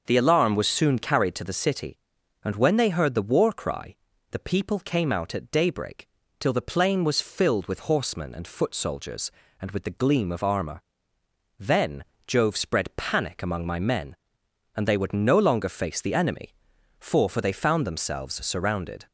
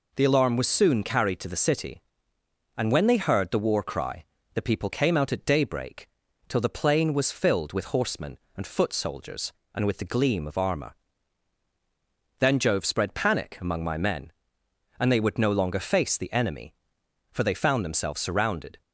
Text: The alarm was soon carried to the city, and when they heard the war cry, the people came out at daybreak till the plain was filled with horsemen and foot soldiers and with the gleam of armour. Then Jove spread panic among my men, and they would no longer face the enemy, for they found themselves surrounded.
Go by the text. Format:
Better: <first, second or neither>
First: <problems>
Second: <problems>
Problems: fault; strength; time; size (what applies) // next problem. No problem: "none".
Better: second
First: starts louder than the rest; until 1.0 s; 6.5 dB // pauses between "daybreak" and "till"; slight; at 6.0 s; 0.32 s long // pauses between "Then" and "Jove"; slight; at 12.0 s; 0.22 s long // says "for" twice; at 17.2 s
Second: pauses between "daybreak" and "till"; at 6.0 s; 0.40 s long